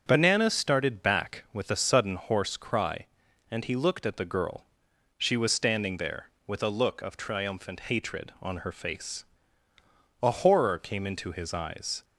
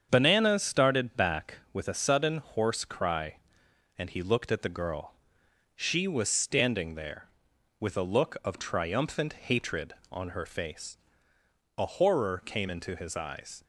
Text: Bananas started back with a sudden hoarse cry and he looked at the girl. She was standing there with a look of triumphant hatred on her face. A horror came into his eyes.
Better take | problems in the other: neither | starts louder than the rest; the same in both

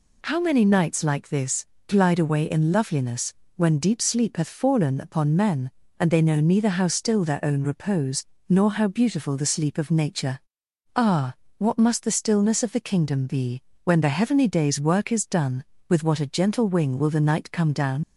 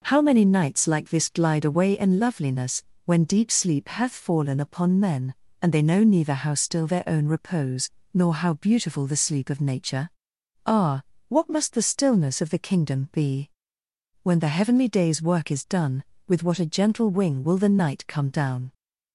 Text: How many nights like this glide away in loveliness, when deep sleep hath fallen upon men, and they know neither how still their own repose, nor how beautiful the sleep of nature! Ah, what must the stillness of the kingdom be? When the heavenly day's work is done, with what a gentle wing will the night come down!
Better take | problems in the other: second | pauses between "this" and "glide"; slight; at 1.6 s; 0.22 s long // leaves "down" unfinished; at 18.0 s; 55 ms

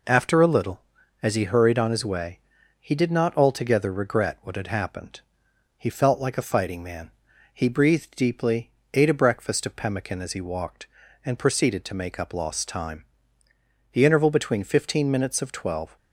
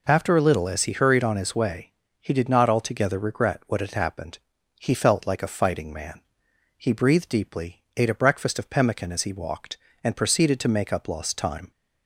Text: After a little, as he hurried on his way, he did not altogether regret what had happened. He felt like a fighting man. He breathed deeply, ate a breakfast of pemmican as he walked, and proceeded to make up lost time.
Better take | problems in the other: second | goes on to say "The interval between fifteen minutes of twelve"; strong; from 13.9 s on; 2.0 s long

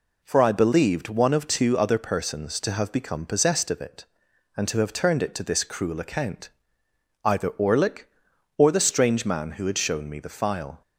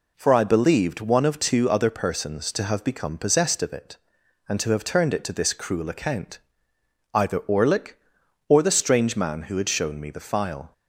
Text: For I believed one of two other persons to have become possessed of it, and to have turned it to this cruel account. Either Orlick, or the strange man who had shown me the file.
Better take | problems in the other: neither | none

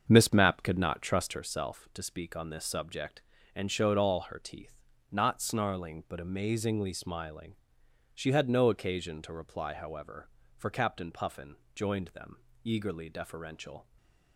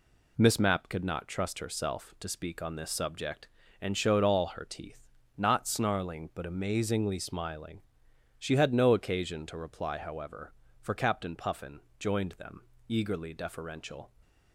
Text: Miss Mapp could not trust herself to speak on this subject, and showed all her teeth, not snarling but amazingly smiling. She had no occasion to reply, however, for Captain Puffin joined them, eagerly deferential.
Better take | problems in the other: second | starts louder than the rest; until 1.5 s; 7 dB // pauses between "Puffin" and "joined"; slight; at 11.5 s; 0.20 s long; slight in the second // stays silent after the last word; slight; from 13.8 s on; 0.5 s long

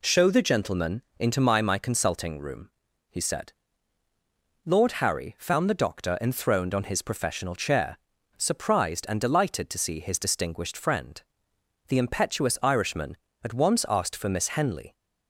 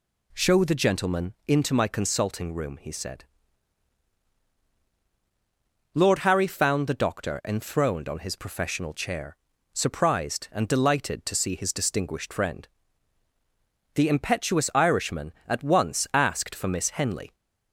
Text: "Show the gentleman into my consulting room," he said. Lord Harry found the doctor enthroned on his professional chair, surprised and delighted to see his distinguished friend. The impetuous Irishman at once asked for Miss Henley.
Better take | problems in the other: second | pauses between "gentleman" and "into"; slight; at 1.0 s; 0.16 s long // says "my" twice; at 1.6 s

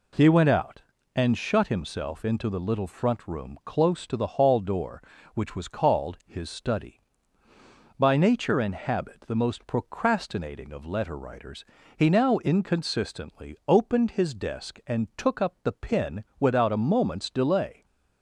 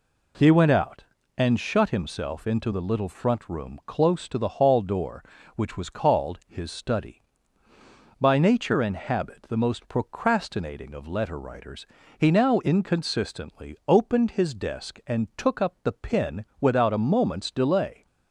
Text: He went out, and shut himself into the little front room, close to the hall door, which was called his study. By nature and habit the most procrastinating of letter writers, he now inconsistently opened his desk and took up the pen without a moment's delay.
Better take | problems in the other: neither | none

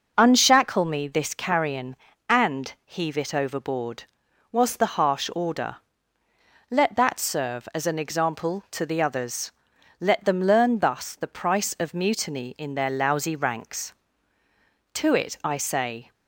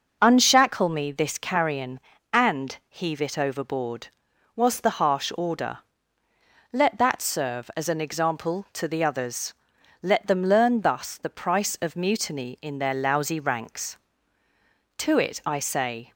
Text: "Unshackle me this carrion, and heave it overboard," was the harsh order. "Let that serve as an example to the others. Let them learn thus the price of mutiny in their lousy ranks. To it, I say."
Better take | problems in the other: neither | none

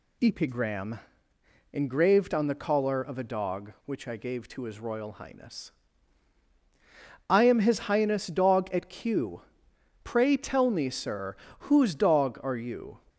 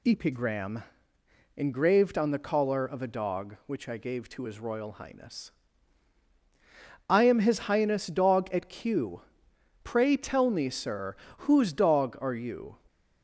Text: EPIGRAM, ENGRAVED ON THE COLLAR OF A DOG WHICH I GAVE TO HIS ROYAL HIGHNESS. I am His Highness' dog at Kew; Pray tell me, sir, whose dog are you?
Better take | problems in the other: neither | none

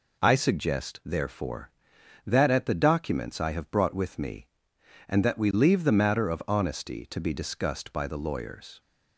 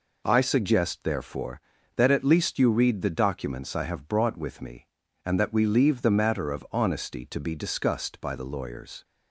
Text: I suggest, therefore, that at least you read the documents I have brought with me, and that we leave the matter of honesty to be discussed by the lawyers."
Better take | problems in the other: second | skips "least you read"; at 2.6 s

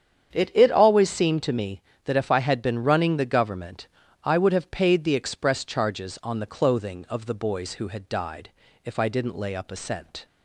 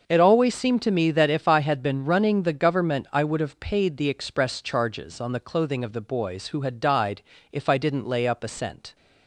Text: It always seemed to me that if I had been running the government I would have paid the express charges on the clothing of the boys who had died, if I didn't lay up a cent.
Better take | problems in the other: second | starts louder than the rest; strong; until 1.3 s; 8 dB // says "It" twice; at 0.5 s // pauses between "government" and "I"; at 3.8 s; 0.38 s long

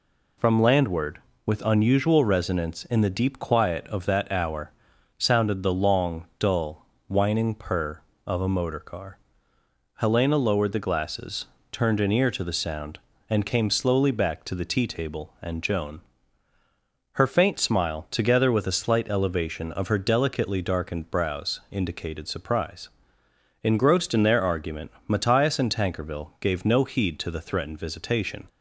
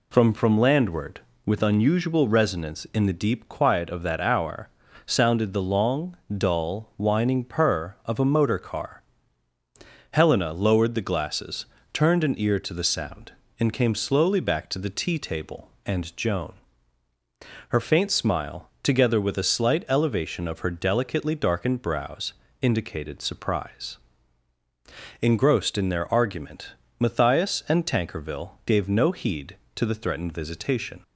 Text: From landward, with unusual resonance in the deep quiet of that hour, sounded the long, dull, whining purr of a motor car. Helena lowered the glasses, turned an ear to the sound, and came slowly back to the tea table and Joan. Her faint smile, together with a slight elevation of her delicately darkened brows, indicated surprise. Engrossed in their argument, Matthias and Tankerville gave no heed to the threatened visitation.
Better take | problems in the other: first | says "From" twice; at 0.3 s

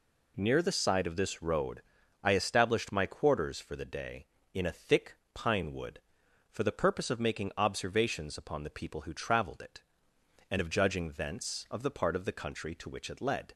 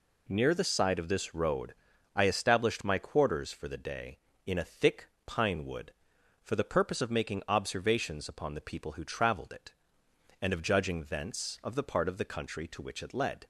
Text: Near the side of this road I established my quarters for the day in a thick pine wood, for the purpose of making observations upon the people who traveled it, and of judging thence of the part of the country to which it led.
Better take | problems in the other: neither | pauses between "road" and "I"; the same in both // pauses between "thick" and "pine"; slight; the same in both

